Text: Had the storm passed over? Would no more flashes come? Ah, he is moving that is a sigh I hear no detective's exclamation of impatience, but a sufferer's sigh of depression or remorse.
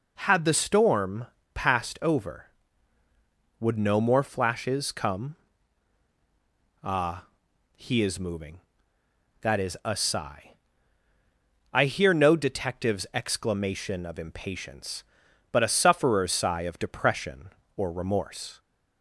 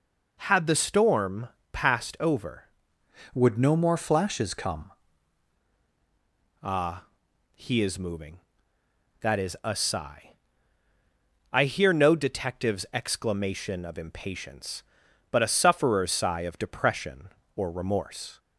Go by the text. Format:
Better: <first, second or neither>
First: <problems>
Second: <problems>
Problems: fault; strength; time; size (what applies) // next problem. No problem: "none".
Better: first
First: pauses between "storm" and "passed"; slight; at 1.2 s; 0.27 s long // pauses between "sigh" and "I"; at 10.5 s; 1.2 s long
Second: pauses between "storm" and "passed"; slight; at 1.4 s; 0.24 s long // changes voice from "Would" to "come"; from 3.3 to 4.9 s; 1.6 s long // pauses between "sigh" and "I"; at 10.3 s; 1.2 s long